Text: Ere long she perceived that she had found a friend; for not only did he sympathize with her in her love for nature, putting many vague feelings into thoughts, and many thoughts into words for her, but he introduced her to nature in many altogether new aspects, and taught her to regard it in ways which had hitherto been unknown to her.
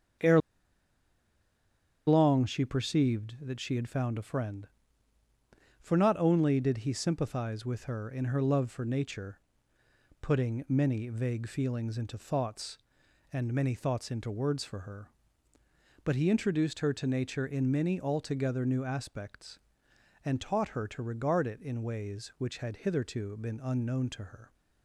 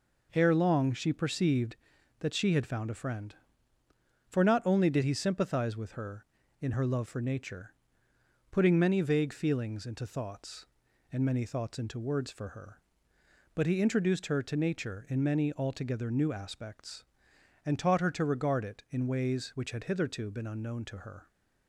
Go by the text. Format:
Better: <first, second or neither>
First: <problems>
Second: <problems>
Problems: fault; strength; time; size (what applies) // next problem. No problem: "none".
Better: second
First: starts louder than the rest; strong; until 2.8 s; 7.5 dB // pauses between "Ere" and "long"; strong; at 0.4 s; 1.6 s long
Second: none